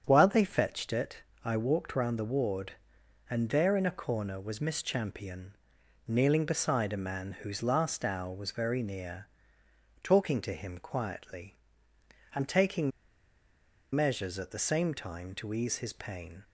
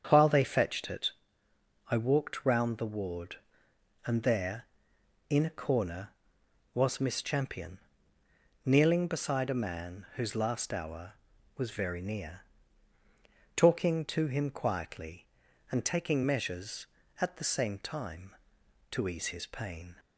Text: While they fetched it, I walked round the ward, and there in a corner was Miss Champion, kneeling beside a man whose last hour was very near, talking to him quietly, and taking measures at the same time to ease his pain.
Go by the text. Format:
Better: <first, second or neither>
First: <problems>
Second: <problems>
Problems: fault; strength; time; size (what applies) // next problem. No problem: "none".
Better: second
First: starts louder than the rest; strong; until 1.0 s; 7.5 dB // pauses between "taking" and "measures"; at 12.9 s; 1.0 s long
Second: starts louder than the rest; strong; until 1.1 s; 7.5 dB